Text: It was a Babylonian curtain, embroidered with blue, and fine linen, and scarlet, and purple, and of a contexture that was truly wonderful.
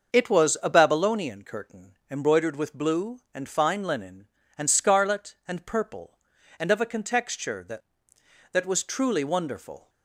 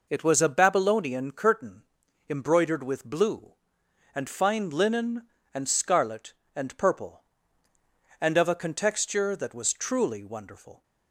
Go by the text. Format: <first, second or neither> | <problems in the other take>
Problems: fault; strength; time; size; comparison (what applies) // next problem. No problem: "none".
second | starts louder than the rest; until 1.2 s; 6.5 dB // says "that" twice; at 8.5 s